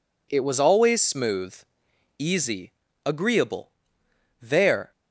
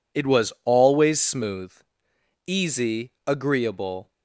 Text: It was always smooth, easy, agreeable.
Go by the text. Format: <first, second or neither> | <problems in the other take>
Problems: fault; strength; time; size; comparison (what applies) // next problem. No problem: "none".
second | goes on to say "There"; from 4.4 s on; 0.50 s long